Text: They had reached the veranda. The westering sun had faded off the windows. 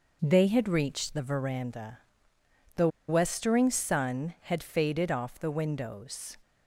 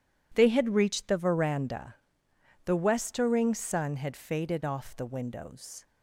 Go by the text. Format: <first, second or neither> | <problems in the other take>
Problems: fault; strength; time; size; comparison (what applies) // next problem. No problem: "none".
second | pauses between "The" and "westering"; slight; at 2.8 s; 0.20 s long